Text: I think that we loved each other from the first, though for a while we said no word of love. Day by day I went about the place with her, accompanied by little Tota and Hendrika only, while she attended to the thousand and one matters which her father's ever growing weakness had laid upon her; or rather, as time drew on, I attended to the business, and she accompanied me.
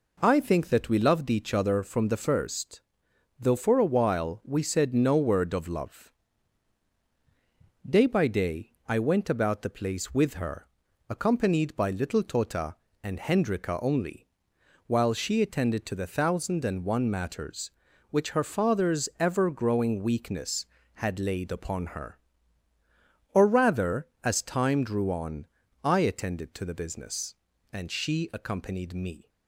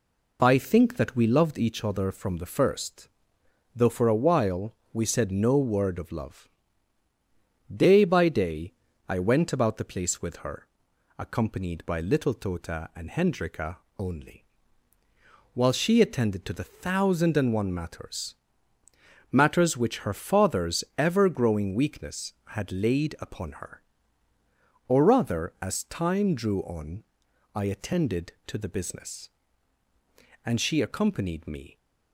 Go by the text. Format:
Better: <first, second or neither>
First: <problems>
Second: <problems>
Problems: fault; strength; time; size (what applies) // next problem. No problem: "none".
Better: first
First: pauses between "day" and "I"; slight; at 8.7 s; 0.16 s long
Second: pauses between "while" and "we"; slight; at 4.7 s; 0.18 s long // pauses between "day" and "I"; slight; at 8.7 s; 0.34 s long // pauses between "Hendrika" and "only"; slight; at 13.7 s; 0.22 s long // says "matters" twice; at 19.3 s